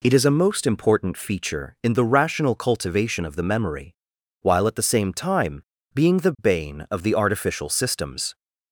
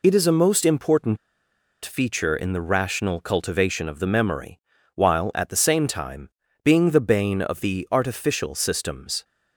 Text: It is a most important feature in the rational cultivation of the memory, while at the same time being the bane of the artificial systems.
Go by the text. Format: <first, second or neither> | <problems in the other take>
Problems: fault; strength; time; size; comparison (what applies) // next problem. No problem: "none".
first | pauses between "important" and "feature"; noticeable; at 1.1 s; 0.66 s long // pauses between "time" and "being"; slight; at 6.3 s; 0.32 s long; slight in the first